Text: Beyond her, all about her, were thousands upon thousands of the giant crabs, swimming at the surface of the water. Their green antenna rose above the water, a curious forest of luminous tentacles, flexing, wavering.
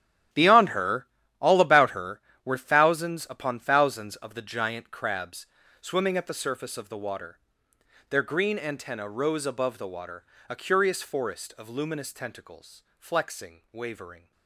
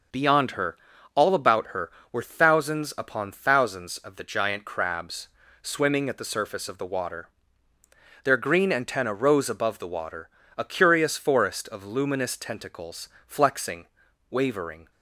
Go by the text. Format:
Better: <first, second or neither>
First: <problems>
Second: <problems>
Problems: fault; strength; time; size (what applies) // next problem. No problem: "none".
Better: second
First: gets quieter; strong; throughout; 14 dB // starts louder than the rest; strong; until 1.6 s; 11.5 dB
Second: starts louder than the rest; noticeable; until 1.5 s; 6 dB